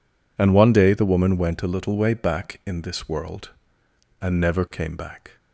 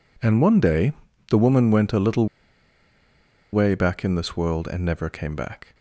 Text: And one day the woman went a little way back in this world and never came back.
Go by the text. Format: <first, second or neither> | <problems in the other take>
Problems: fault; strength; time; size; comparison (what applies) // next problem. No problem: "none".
first | pauses between "day" and "the"; slight; at 0.9 s; 0.36 s long // pauses between "little" and "way"; strong; at 2.2 s; 1.2 s long